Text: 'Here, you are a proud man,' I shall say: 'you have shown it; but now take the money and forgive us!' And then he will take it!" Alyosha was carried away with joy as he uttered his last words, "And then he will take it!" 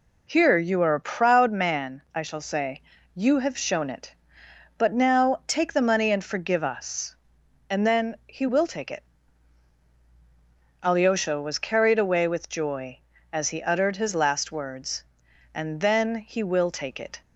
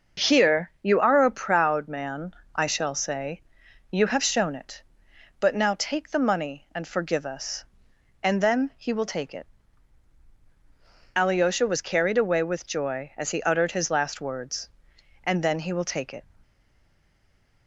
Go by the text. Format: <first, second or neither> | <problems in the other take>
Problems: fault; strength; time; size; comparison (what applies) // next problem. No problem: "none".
first | stays silent after the last word; noticeable; from 16.4 s on; 1.2 s long